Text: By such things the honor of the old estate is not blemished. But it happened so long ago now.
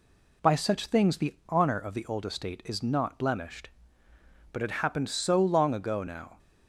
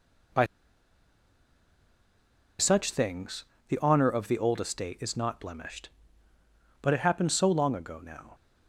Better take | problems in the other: first | pauses between "By" and "such"; strong; at 0.4 s; 2.1 s long // pauses between "things" and "the"; slight; at 3.4 s; 0.26 s long

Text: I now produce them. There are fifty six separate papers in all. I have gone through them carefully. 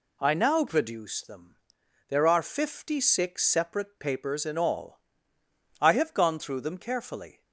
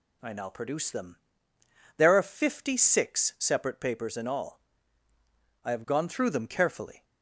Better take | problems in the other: neither | none

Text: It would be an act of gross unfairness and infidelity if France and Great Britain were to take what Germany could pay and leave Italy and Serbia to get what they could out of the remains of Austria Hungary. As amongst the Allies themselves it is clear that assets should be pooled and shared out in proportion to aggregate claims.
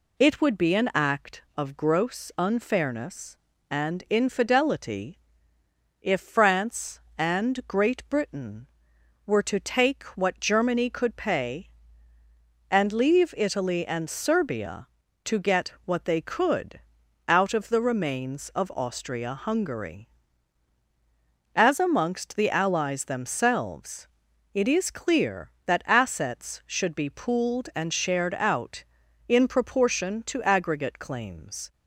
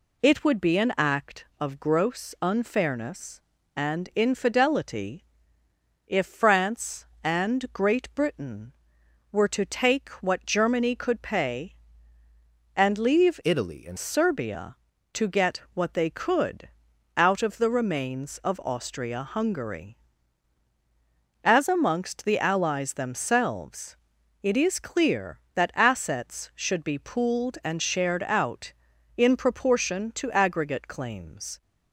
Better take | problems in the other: first | pauses between "infidelity" and "if"; noticeable; at 5.2 s; 0.84 s long; noticeable in the first // changes voice from "Italy" to "and"; from 13.4 to 13.9 s; 0.5 s long // pauses between "could" and "out"; noticeable; at 16.6 s; 0.46 s long; noticeable in the first // pauses between "themselves" and "it"; at 23.9 s; 0.44 s long; also in the first

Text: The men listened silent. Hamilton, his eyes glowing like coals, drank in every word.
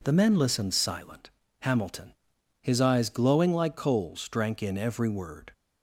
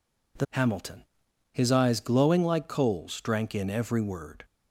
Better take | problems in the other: first | skips "men listened silent"; at 0.4 s

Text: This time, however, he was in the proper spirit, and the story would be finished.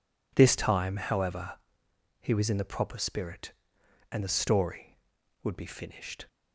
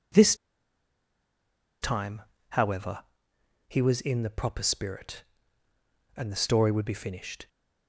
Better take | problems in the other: first | pauses between "This" and "time"; strong; at 0.3 s; 1.4 s long

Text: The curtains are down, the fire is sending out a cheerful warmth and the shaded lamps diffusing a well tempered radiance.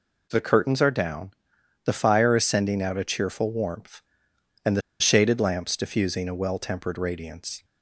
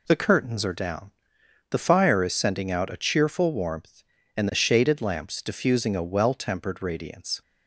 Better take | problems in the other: second | pauses between "the" and "shaded"; slight; at 4.8 s; 0.19 s long

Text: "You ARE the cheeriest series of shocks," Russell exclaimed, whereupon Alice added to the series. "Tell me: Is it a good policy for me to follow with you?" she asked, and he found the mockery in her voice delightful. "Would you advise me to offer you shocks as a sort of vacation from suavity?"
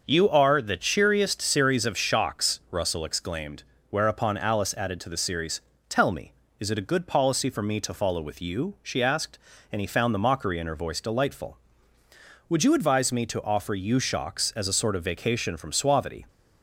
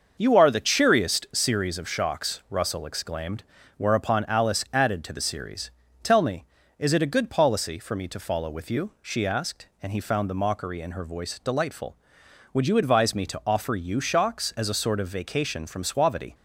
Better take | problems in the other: neither | starts louder than the rest; the same in both

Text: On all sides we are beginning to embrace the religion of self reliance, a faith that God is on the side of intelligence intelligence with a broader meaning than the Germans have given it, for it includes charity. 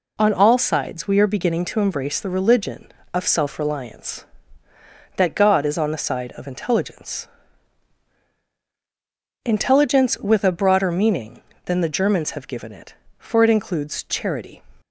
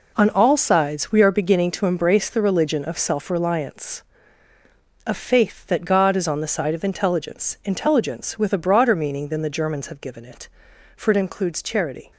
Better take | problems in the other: second | skips "a faith"; at 4.7 s // pauses between "intelligence" and "intelligence"; strong; at 7.2 s; 2.1 s long

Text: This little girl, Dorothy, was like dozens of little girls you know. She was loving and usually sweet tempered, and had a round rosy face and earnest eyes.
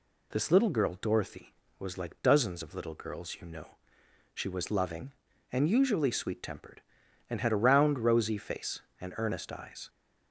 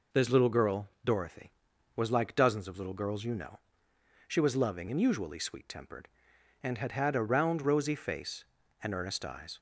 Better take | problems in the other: first | says "had" twice; at 6.9 s

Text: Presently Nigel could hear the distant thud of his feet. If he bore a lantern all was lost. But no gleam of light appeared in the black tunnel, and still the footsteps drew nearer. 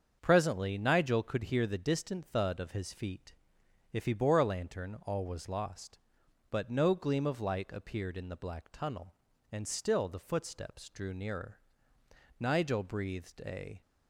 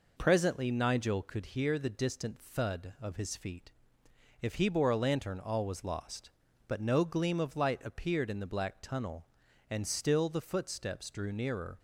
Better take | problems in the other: second | starts louder than the rest; until 1.2 s; 7 dB // goes on to say "Nigel breathed a"; from 12.3 s on; 1.4 s long

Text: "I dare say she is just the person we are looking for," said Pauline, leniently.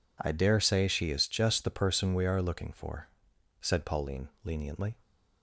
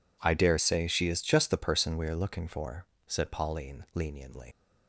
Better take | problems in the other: first | leaves "leniently" unfinished; at 4.5 s; 50 ms

